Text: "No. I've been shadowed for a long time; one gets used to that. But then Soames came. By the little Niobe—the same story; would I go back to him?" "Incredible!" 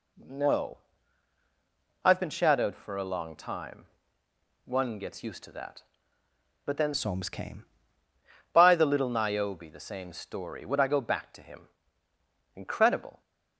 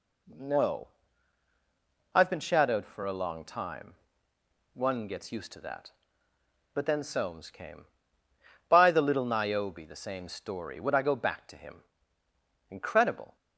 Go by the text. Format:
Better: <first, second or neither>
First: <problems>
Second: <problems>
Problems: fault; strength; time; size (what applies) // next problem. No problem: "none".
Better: second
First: changes voice from "Soames" to "came"; from 6.9 to 7.6 s; 0.7 s long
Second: none